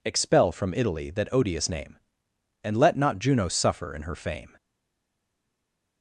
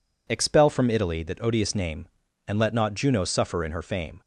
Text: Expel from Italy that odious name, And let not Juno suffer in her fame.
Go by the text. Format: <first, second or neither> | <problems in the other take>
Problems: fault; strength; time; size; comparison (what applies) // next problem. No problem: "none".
second | stays silent after the last word; noticeable; from 4.5 s on; 1.5 s long